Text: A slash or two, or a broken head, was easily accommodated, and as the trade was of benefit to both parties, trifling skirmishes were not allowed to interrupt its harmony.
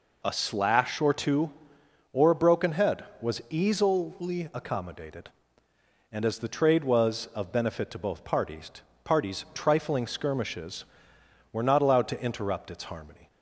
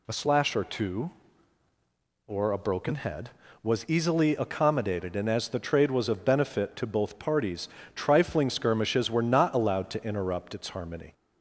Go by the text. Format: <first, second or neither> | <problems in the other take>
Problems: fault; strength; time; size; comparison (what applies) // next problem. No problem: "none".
second | says "parties" twice; at 9.0 s